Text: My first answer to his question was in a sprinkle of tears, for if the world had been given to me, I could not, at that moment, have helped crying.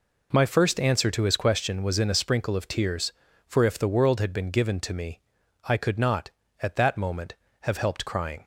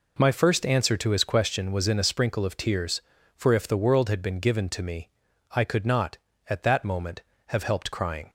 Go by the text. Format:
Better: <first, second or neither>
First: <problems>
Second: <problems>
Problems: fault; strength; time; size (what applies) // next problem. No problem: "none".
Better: neither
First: none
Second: none